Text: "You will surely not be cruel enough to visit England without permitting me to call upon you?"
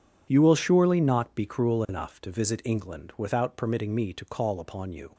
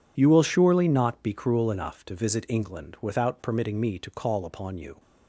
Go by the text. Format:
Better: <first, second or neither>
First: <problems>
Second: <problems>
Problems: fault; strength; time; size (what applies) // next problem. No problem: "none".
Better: neither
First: none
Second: none